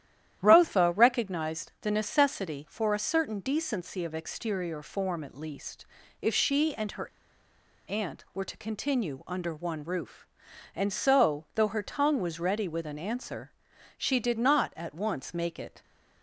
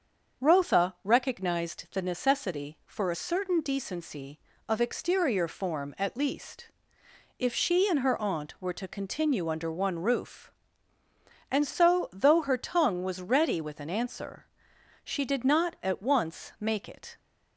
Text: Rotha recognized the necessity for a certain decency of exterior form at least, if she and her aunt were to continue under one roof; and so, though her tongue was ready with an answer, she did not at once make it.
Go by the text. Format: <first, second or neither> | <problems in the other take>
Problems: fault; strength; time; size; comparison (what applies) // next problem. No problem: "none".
second | starts louder than the rest; strong; until 1.4 s; 11.5 dB; also in the second // pauses between "her" and "aunt"; noticeable; at 7.0 s; 0.78 s long